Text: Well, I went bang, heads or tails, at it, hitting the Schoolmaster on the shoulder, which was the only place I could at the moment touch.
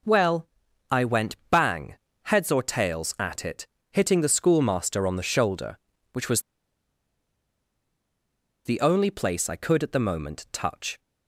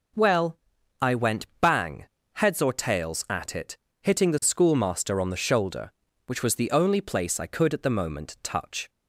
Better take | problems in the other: second | pauses between "was" and "the"; strong; at 6.4 s; 2.2 s long

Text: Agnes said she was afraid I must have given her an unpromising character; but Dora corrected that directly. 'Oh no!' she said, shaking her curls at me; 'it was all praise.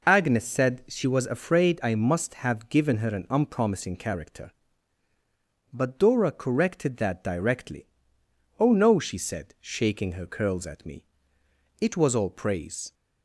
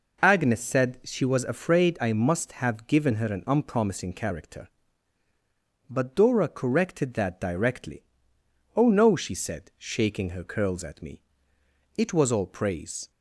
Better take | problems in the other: neither | none

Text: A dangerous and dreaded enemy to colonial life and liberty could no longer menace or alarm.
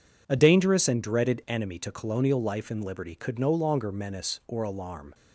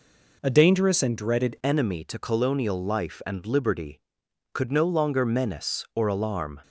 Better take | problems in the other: first | changes voice at "enemy"; from 1.6 s on; 5.0 s long

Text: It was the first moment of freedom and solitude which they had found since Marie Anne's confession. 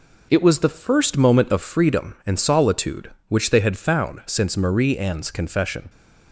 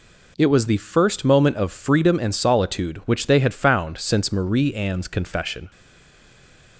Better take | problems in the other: first | stays silent after the last word; from 5.7 s on; 1.0 s long

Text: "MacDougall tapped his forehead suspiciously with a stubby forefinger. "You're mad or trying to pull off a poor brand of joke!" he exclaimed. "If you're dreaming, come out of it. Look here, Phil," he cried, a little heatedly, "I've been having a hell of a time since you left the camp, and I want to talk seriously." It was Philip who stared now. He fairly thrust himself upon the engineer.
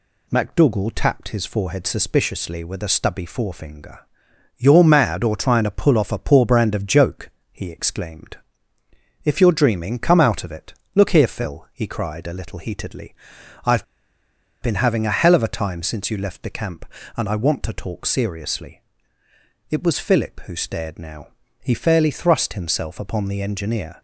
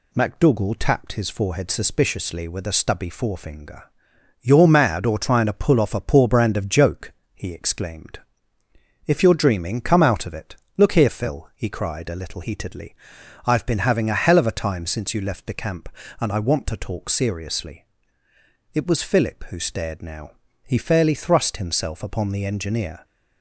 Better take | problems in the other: second | pauses between "I've" and "been"; noticeable; at 13.8 s; 0.77 s long

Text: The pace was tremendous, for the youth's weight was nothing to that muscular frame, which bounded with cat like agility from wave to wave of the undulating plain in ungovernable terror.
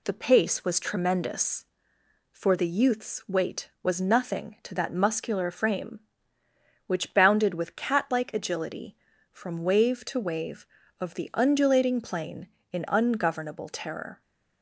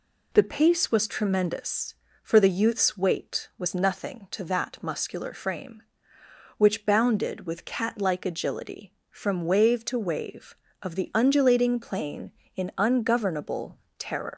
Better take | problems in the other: first | pauses between "ungovernable" and "terror"; slight; at 13.7 s; 0.22 s long // leaves "terror" unfinished; at 14.3 s; 100 ms

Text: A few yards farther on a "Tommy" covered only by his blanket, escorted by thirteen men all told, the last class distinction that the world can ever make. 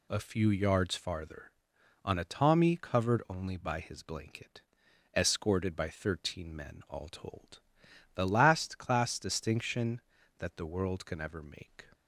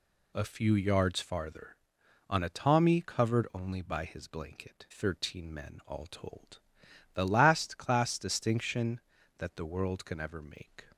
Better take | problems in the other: first | skips "escorted by"; at 4.8 s

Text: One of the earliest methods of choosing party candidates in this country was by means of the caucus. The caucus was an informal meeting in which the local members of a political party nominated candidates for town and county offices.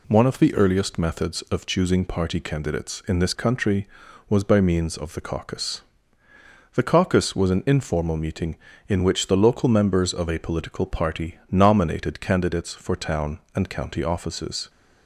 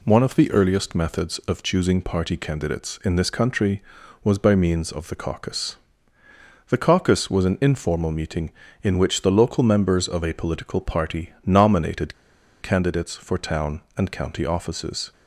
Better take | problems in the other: first | pauses between "nominated" and "candidates"; noticeable; at 12.1 s; 0.48 s long

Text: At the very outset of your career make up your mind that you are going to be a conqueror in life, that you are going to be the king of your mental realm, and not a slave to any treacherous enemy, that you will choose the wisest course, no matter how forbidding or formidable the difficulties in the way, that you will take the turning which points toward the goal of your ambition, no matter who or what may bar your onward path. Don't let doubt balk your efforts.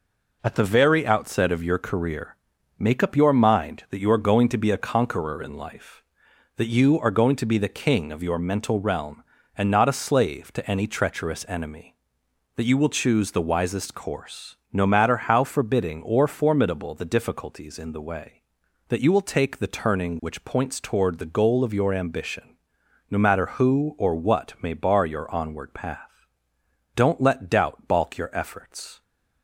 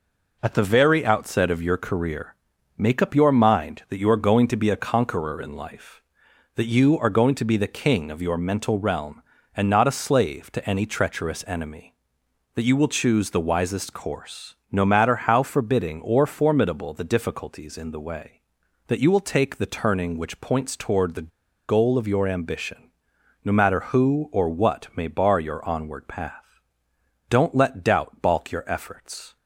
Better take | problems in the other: first | pauses between "career" and "make"; at 2.3 s; 0.40 s long; also in the first // pauses between "the" and "goal"; at 21.2 s; 0.40 s long

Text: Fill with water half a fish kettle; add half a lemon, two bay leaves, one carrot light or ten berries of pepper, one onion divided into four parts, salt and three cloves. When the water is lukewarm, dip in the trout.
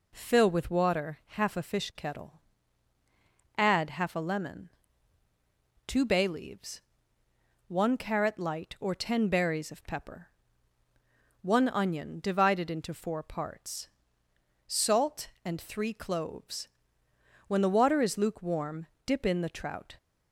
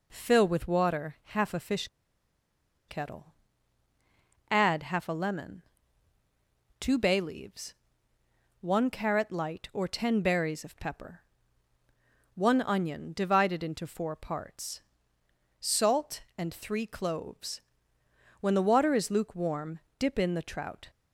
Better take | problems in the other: first | pauses between "fish" and "kettle"; at 1.8 s; 1.0 s long

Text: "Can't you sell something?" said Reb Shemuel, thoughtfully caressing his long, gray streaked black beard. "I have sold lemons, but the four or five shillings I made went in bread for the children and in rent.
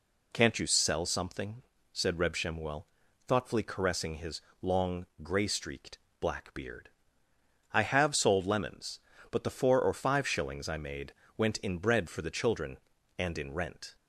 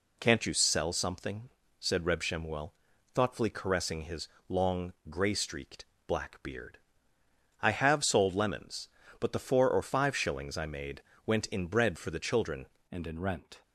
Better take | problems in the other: first | pauses between "his" and "long"; slight; at 4.2 s; 0.20 s long; slight in the first // pauses between "streaked" and "black"; slight; at 5.8 s; 0.22 s long; slight in the first // pauses between "made" and "went"; slight; at 11.0 s; 0.22 s long; slight in the first // changes voice at "and"; from 12.8 s on; 0.8 s long

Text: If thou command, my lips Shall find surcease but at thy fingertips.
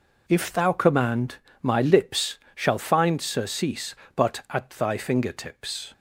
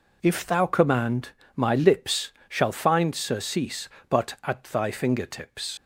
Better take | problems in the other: first | pauses between "lips" and "Shall"; slight; at 2.3 s; 0.16 s long; slight in the first // leaves "fingertips" unfinished; at 5.7 s; 90 ms

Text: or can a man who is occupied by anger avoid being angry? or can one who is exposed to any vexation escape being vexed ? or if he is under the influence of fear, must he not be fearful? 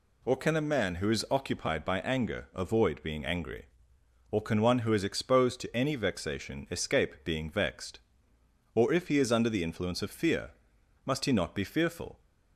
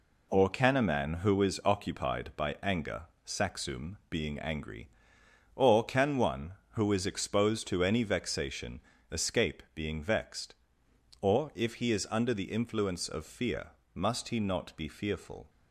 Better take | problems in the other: first | says "saxum" for "avoid"; at 3.2 s // pauses between "vexation" and "escape"; slight; at 8.7 s; 0.30 s long

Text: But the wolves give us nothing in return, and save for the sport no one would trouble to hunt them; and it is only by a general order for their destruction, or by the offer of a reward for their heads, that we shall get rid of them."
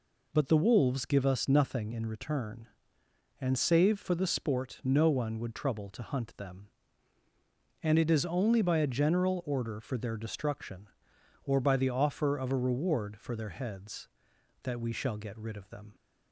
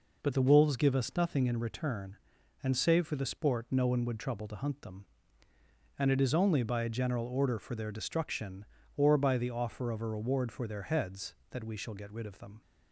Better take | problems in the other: neither | none

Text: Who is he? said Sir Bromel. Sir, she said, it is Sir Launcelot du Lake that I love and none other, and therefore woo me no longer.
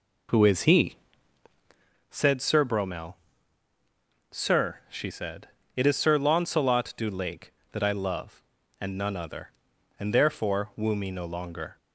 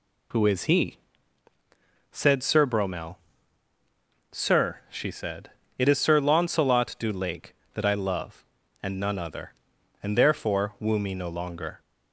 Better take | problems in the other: second | starts louder than the rest; until 1.9 s; 4 dB

